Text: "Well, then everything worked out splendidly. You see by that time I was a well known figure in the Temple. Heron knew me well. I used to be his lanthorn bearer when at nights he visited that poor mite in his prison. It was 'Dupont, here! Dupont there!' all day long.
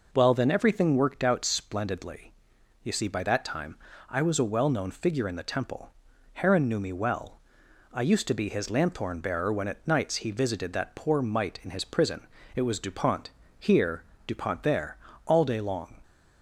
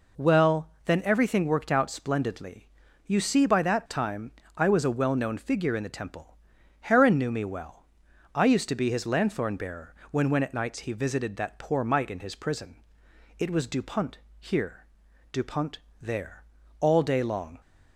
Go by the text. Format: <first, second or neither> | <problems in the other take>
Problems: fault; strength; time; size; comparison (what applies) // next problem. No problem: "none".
first | pauses between "time" and "I"; slight; at 4.3 s; 0.24 s long; slight in the first // pauses between "bearer" and "when"; slight; at 9.9 s; 0.16 s long // says "when" twice; at 10.2 s // pauses between "Dupont" and "there"; slight; at 15.7 s; 0.22 s long